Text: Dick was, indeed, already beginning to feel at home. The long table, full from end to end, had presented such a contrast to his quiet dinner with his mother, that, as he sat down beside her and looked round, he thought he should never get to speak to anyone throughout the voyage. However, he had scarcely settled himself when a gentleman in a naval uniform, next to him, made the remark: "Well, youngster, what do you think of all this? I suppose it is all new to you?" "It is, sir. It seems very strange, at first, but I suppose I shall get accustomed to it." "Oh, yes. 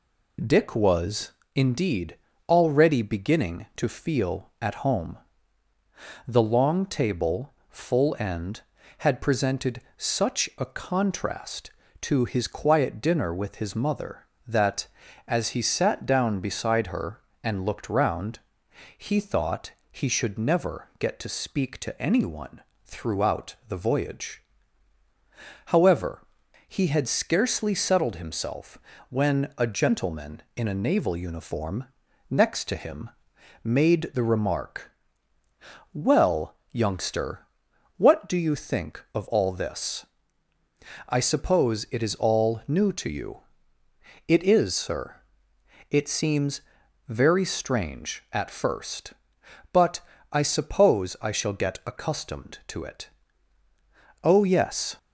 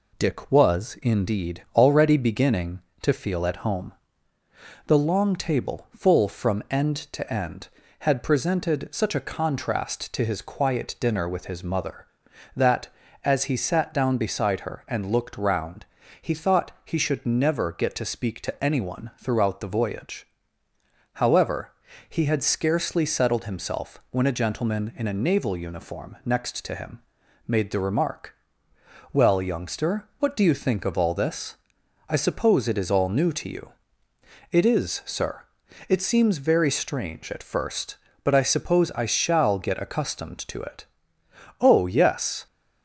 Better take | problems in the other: second | skips "from end to"; at 8.1 s // pauses between "presented" and "such"; slight; at 9.8 s; 0.16 s long // pauses between "thought" and "he"; slight; at 19.7 s; 0.20 s long // pauses between "anyone" and "throughout"; slight; at 22.6 s; 0.22 s long // pauses between "himself" and "when"; slight; at 28.7 s; 0.32 s long // pauses between "seems" and "very"; noticeable; at 46.6 s; 0.46 s long // pauses between "but" and "I"; slight; at 50.0 s; 0.30 s long

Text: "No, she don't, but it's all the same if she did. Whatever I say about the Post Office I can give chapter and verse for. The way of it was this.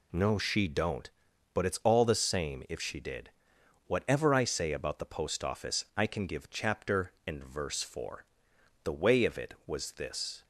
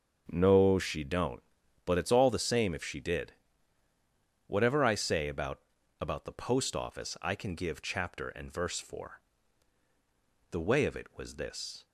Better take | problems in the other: first | starts louder than the rest; until 1.2 s; 6.5 dB // says "about" twice; at 6.0 s

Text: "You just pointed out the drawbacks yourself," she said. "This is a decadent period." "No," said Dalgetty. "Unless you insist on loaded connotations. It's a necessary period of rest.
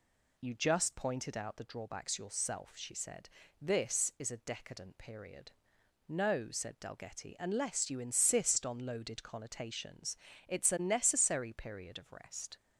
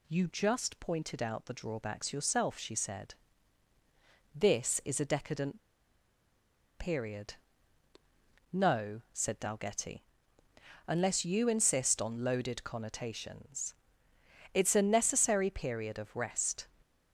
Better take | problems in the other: first | pauses between "decadent" and "period"; at 5.6 s; 1.1 s long

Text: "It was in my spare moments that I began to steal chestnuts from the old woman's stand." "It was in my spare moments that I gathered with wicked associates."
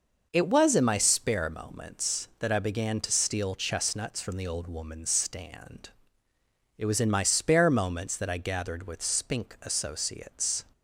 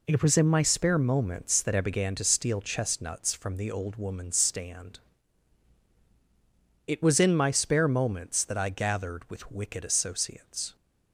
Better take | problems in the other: second | says "spink" for "wicked"; at 9.0 s

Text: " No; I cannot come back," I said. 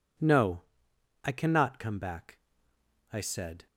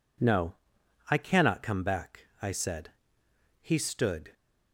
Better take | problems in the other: first | goes on to say "He stood"; noticeable; from 3.6 s on; 0.72 s long

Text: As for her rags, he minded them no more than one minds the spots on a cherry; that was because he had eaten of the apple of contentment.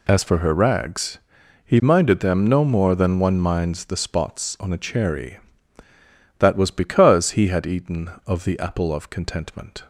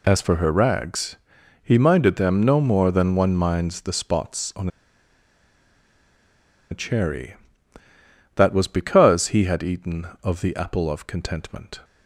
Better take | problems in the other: first | pauses between "on" and "a"; strong; at 4.6 s; 2.0 s long

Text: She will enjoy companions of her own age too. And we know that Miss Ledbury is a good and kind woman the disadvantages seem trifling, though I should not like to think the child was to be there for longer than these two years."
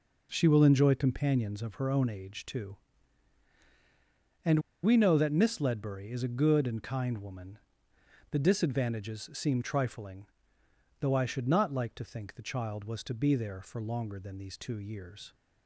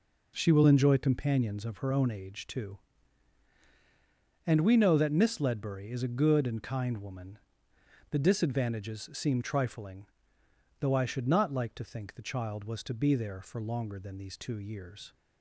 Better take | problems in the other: second | pauses between "And" and "we"; slight; at 4.6 s; 0.22 s long // pauses between "woman" and "the"; noticeable; at 7.5 s; 0.74 s long; noticeable in the second

